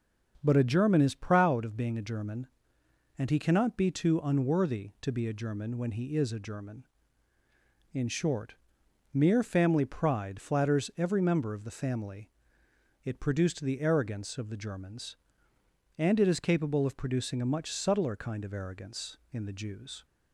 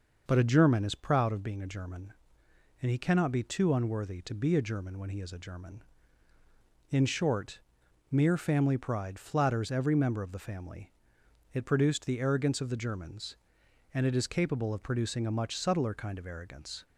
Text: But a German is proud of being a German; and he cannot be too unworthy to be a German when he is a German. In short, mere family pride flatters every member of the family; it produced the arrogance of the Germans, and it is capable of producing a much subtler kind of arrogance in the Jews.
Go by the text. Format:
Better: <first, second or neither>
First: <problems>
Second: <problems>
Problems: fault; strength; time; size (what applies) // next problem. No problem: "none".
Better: first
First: starts louder than the rest; until 1.4 s; 7 dB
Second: starts louder than the rest; noticeable; until 1.2 s; 6 dB // stops before "in the Jews"; at 16.8 s